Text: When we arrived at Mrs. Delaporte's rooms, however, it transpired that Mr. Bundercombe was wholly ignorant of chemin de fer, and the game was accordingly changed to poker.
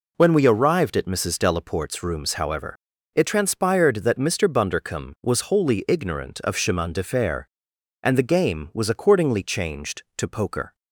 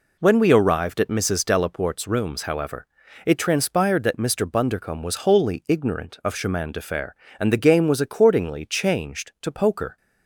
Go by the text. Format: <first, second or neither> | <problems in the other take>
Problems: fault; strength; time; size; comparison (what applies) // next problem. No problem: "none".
neither | none